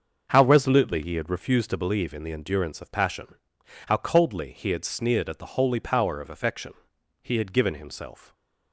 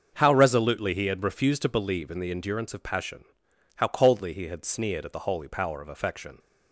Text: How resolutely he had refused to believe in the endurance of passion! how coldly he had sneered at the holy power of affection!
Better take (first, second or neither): second